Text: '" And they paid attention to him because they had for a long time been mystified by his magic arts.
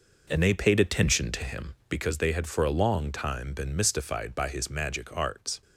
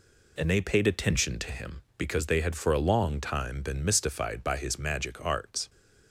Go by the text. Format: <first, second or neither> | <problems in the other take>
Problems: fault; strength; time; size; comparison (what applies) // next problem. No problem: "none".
second | starts louder than the rest; noticeable; until 2.1 s; 5 dB